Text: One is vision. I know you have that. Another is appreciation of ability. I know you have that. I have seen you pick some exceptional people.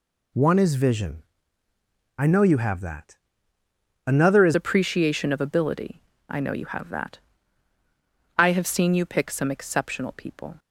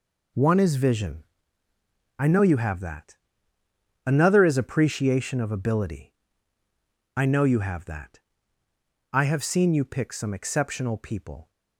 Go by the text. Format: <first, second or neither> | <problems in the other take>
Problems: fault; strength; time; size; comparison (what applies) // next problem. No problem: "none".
second | changes voice at "appreciation"; from 4.5 s on; 6.0 s long